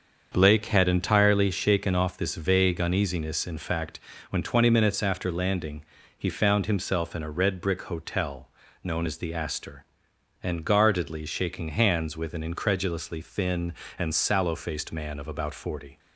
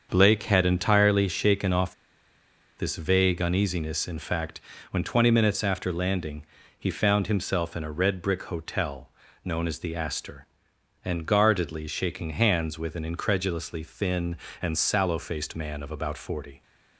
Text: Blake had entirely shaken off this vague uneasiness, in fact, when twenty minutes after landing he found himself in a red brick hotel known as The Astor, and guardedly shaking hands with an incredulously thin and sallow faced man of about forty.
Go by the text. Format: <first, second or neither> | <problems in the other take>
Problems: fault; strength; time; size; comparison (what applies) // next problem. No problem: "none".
first | starts louder than the rest; until 1.1 s; 7 dB; also in the first // pauses between "off" and "this"; noticeable; at 1.9 s; 0.83 s long // pauses between "landing" and "he"; slight; at 6.4 s; 0.32 s long; slight in the first // pauses between "hotel" and "known"; slight; at 9.0 s; 0.34 s long; slight in the first